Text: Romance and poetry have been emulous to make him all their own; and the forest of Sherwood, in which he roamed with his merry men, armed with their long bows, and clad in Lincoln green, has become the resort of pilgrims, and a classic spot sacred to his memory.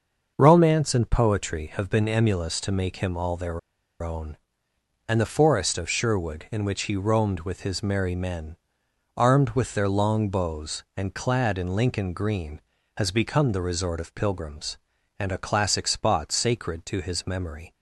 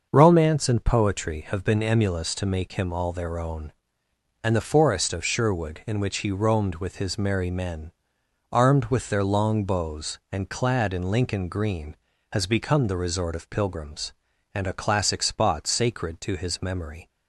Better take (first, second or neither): second